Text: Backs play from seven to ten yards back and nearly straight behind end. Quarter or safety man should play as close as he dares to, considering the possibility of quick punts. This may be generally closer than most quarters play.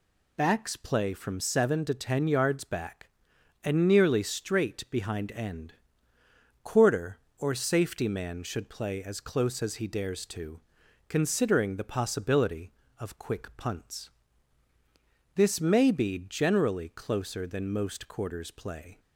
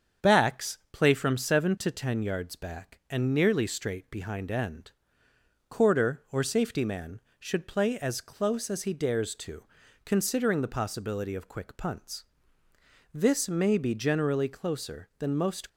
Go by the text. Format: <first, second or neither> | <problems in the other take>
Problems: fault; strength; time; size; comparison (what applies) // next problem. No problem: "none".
first | starts louder than the rest; strong; until 1.3 s; 7.5 dB // stops before "quarters play"; at 15.6 s